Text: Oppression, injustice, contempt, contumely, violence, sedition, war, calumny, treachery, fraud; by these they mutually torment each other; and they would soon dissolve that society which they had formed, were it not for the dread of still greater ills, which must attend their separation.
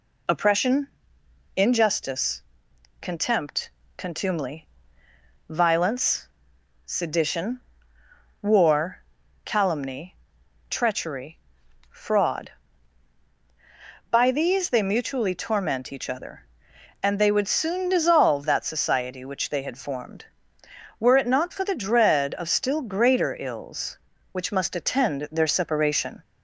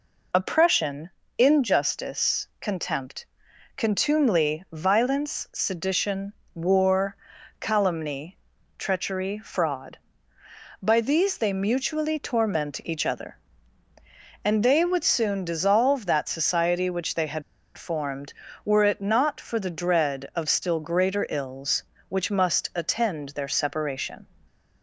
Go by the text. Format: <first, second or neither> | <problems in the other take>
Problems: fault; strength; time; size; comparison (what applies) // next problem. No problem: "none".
first | pauses between "had" and "formed"; slight; at 17.4 s; 0.35 s long